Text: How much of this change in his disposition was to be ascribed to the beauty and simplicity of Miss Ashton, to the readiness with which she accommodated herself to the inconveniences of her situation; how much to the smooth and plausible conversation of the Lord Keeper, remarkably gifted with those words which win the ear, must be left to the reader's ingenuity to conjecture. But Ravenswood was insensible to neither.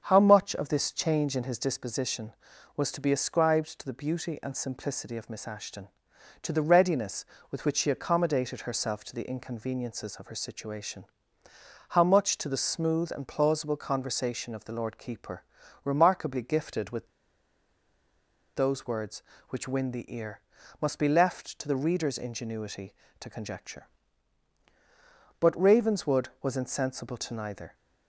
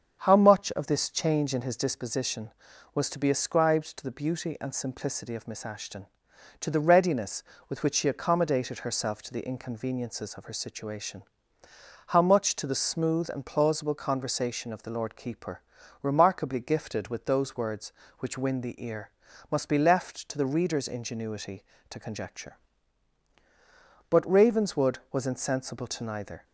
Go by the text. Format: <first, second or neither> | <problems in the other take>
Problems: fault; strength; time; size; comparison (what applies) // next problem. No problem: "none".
second | starts louder than the rest; strong; until 1.1 s; 7.5 dB; strong in the second // pauses between "with" and "those"; strong; at 17.0 s; 1.4 s long